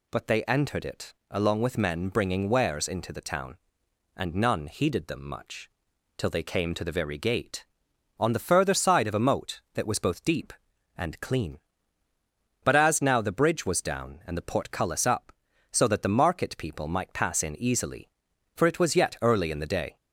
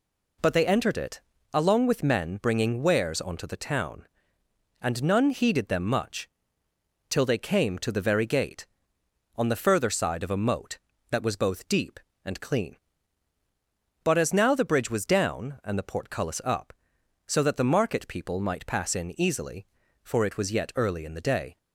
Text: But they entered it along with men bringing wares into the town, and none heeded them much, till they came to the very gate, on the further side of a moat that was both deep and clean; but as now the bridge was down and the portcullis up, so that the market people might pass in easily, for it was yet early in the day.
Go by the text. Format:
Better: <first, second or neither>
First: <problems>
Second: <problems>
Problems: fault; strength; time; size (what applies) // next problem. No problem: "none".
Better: first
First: pauses between "it" and "along"; slight; at 1.1 s; 0.16 s long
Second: pauses between "it" and "along"; slight; at 1.2 s; 0.30 s long // says "onto" for "into"; at 3.1 s